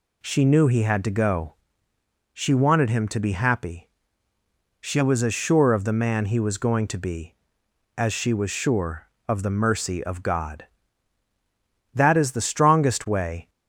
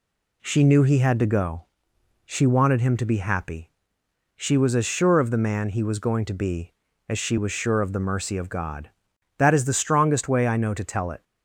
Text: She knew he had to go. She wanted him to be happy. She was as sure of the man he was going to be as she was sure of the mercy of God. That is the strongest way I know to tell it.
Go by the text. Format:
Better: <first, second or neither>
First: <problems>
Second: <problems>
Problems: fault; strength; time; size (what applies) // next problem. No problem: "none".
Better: second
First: stops before "I know to tell it"; at 13.4 s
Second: none